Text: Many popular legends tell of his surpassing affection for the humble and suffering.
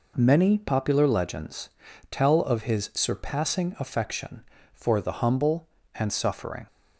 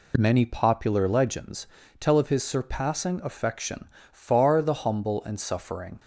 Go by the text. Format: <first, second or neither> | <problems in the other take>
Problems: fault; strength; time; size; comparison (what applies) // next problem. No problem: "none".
first | pauses between "legends" and "tell"; slight; at 1.6 s; 0.34 s long; also in the first // says "far" for "for"; at 4.1 s